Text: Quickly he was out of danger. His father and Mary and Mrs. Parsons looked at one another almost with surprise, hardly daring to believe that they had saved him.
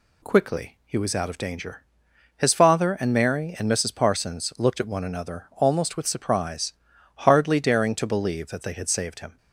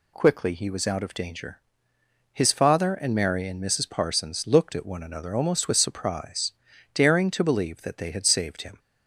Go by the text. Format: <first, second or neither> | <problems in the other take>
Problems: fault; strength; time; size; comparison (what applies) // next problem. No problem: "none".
first | skips "hardly"; at 6.7 s